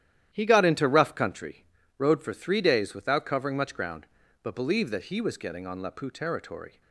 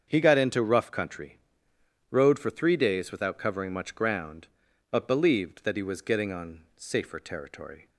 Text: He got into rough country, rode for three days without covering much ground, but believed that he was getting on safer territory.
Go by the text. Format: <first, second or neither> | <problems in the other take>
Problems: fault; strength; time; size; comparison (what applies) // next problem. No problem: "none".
second | starts louder than the rest; strong; until 1.3 s; 11.5 dB; strong in the second // says "lapu" for "safer"; at 5.8 s